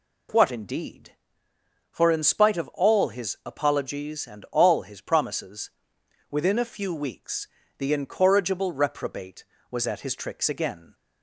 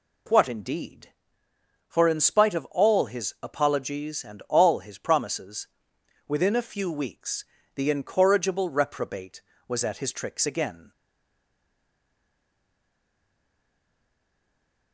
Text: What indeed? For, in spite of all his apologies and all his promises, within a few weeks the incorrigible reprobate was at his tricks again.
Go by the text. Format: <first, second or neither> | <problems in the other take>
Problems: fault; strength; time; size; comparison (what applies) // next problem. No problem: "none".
first | pauses between "weeks" and "the"; slight; at 7.4 s; 0.30 s long; slight in the first // stays silent after the last word; strong; from 10.9 s on; 4.0 s long